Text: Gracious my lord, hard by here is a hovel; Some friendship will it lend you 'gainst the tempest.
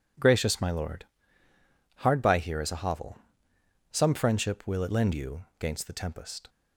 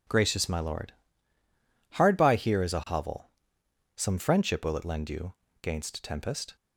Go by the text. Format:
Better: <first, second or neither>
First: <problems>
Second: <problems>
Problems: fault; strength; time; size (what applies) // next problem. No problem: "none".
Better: first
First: none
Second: pauses between "you" and "gainst"; slight; at 5.3 s; 0.28 s long // skips "the"; at 6.0 s